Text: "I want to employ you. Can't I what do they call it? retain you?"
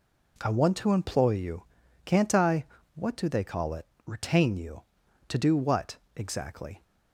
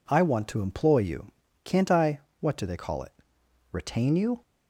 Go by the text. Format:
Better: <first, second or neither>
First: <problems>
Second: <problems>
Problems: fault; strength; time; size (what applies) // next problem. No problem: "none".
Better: second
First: pauses between "I" and "what"; slight; at 2.6 s; 0.30 s long // goes on to say "To do what exactly"; from 5.2 s on; 1.5 s long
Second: pauses between "I" and "what"; slight; at 2.1 s; 0.20 s long